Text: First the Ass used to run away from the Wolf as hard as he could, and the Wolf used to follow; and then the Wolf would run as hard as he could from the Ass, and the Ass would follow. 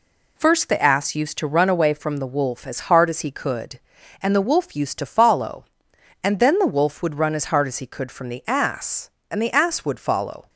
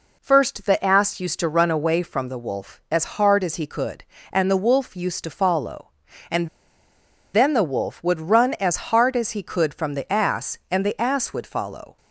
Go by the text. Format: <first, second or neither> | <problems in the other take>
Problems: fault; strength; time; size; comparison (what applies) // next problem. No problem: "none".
first | pauses between "and" and "then"; noticeable; at 6.4 s; 0.86 s long